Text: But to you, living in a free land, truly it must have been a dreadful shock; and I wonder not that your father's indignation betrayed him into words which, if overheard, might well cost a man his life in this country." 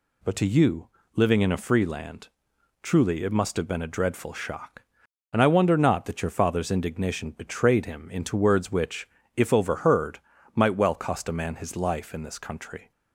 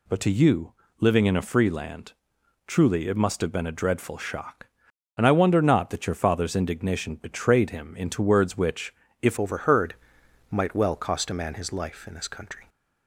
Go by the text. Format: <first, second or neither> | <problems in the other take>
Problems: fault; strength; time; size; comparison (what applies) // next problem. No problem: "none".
first | changes voice at "overheard"; from 9.3 s on; 3.3 s long